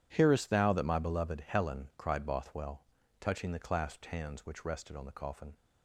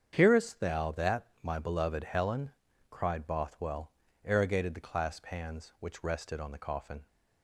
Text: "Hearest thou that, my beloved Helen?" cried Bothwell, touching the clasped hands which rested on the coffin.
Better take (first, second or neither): first